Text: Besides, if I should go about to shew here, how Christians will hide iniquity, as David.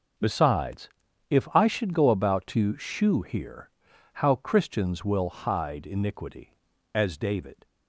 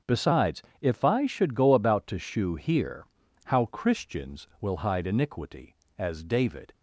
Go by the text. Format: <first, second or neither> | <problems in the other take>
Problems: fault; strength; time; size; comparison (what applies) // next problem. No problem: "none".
neither | starts louder than the rest; the same in both